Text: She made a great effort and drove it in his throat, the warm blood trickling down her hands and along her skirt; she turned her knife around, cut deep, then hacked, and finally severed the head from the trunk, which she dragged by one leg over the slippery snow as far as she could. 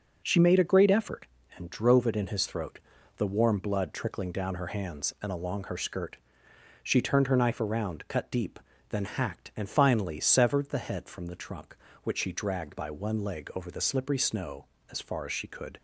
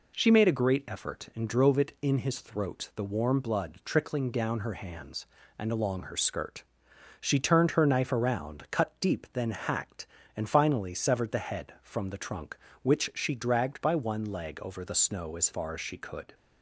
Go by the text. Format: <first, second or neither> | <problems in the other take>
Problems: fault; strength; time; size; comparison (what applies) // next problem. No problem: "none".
first | skips "slippery"; at 14.9 s